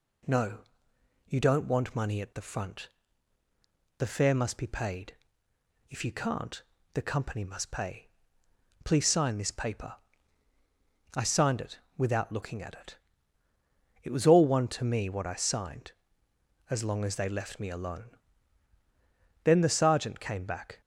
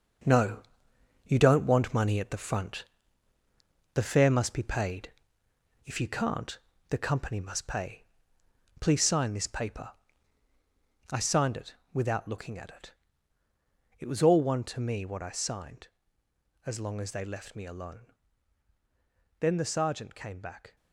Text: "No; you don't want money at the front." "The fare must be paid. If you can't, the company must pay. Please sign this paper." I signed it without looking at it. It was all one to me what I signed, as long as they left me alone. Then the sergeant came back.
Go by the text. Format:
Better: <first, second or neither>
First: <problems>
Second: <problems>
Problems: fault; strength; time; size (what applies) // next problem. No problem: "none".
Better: first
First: pauses between "it" and "without"; slight; at 11.7 s; 0.18 s long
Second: gets quieter; strong; throughout; 7.5 dB // pauses between "it" and "without"; slight; at 11.7 s; 0.18 s long